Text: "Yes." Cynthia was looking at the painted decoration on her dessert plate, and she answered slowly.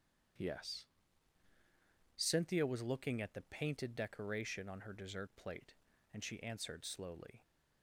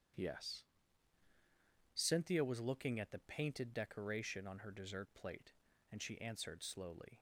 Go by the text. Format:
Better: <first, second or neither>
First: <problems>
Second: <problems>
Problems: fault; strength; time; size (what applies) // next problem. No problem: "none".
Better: neither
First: starts louder than the rest; strong; until 2.6 s; 8.5 dB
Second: starts louder than the rest; strong; until 2.4 s; 8.5 dB